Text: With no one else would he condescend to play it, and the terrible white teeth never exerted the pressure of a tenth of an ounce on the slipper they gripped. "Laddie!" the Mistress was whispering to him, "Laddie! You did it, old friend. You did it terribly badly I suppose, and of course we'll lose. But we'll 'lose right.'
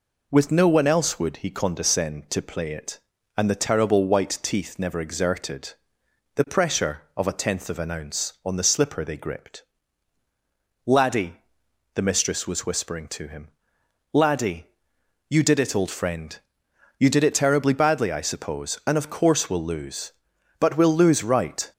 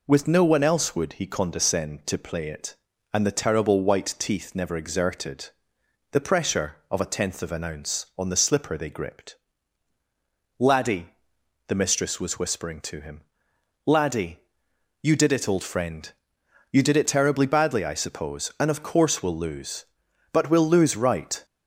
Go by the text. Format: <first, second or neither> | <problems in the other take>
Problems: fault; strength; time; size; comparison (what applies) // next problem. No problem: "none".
neither | pauses between "exerted" and "the"; noticeable; the same in both